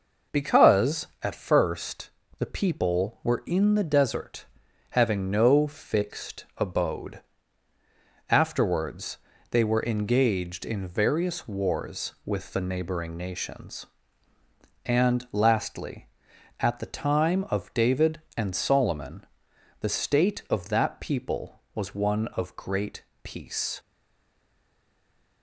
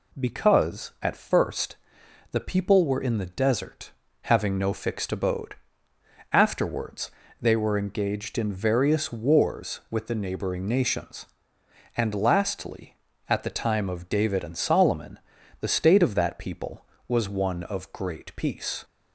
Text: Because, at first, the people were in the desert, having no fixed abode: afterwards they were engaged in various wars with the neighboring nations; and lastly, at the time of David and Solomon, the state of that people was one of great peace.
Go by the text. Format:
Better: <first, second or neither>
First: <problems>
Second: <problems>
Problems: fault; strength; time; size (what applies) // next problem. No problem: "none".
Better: second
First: pauses between "afterwards" and "they"; slight; at 9.1 s; 0.32 s long // pauses between "great" and "peace"; slight; at 23.0 s; 0.22 s long // stays silent after the last word; noticeable; from 23.7 s on; 1.7 s long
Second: pauses between "afterwards" and "they"; slight; at 7.1 s; 0.30 s long